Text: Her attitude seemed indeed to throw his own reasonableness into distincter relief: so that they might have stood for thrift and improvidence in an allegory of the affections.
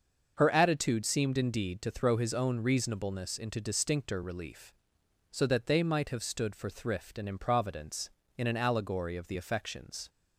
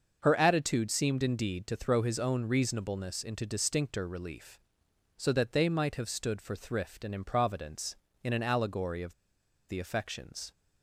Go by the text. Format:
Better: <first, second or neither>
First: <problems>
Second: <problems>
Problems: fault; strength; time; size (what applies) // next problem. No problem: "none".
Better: first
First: starts louder than the rest; until 1.3 s; 6.5 dB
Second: starts louder than the rest; until 1.2 s; 6.5 dB // pauses between "of" and "the"; noticeable; at 9.1 s; 0.56 s long